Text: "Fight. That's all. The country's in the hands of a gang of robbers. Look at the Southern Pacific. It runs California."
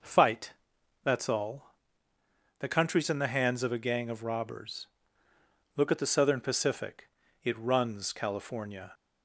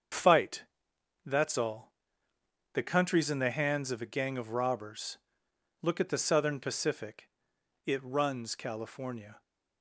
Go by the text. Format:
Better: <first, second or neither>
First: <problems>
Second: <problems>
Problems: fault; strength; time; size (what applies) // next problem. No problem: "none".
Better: first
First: none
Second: loses the start of "Fight"; at 0.1 s; 50 ms // starts louder than the rest; strong; until 1.7 s; 7 dB